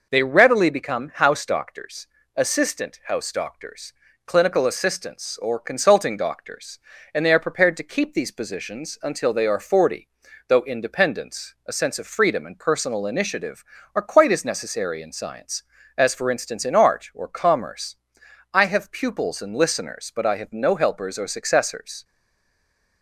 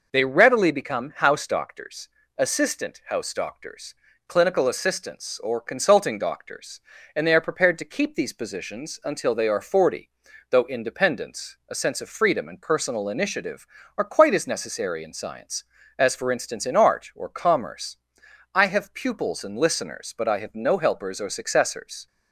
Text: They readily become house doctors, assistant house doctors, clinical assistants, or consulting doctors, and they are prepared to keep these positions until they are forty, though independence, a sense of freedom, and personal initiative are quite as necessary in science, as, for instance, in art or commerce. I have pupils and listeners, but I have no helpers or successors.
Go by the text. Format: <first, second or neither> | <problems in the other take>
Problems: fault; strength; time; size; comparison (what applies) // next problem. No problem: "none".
second | stays silent after the last word; from 22.0 s on; 1.0 s long